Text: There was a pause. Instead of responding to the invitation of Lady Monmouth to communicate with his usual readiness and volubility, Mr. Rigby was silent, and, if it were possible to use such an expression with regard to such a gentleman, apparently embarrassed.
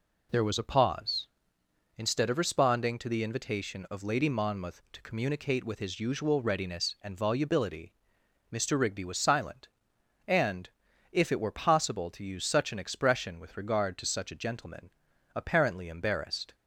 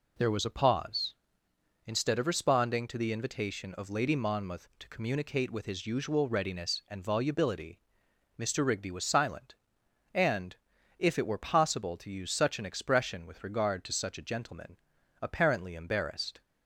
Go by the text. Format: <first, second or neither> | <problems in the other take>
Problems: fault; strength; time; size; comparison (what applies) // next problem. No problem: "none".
neither | none